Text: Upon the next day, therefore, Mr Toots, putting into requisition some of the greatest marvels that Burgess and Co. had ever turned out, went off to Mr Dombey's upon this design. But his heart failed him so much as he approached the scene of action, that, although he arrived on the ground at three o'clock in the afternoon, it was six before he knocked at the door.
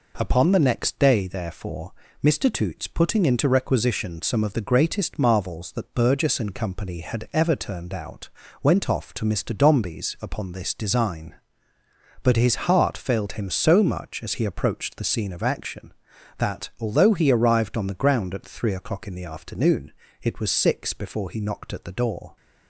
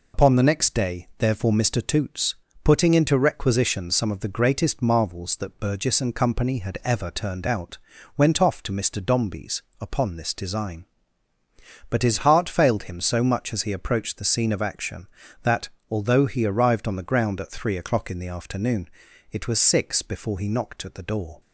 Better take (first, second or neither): first